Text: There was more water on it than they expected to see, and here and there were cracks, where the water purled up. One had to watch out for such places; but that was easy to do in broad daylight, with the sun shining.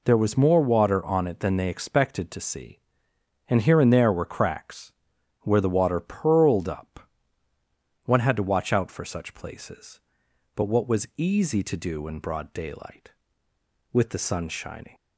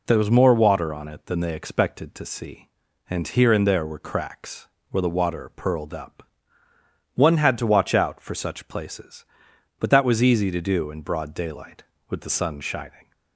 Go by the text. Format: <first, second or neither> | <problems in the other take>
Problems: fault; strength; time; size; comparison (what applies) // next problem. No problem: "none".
second | says "what" for "that"; at 10.6 s